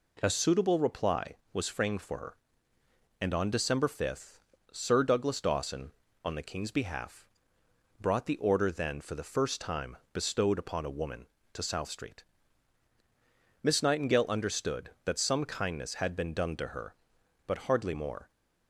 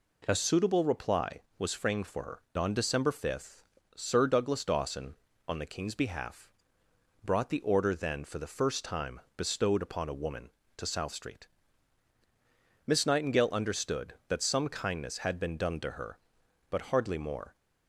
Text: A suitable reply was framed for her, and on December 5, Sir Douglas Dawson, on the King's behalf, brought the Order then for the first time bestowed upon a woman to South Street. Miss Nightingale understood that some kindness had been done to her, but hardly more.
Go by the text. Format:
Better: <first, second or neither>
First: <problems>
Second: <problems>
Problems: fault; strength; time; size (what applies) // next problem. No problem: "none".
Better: first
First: pauses between "time" and "bestowed"; slight; at 9.9 s; 0.16 s long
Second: skips "and"; at 2.4 s // pauses between "time" and "bestowed"; slight; at 9.1 s; 0.16 s long